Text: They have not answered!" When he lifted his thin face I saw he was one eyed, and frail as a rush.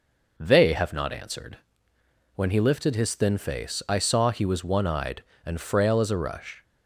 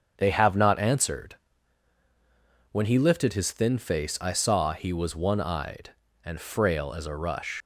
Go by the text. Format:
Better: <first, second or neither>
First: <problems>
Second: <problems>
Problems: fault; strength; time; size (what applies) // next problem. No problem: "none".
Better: first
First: none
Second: starts louder than the rest; strong; until 1.1 s; 7.5 dB // leaves "rush" unfinished; at 7.6 s; 70 ms